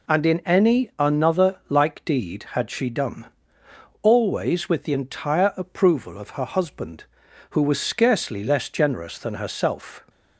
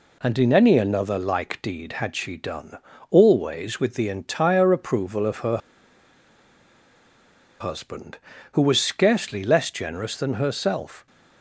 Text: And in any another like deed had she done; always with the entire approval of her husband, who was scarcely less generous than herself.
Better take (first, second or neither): first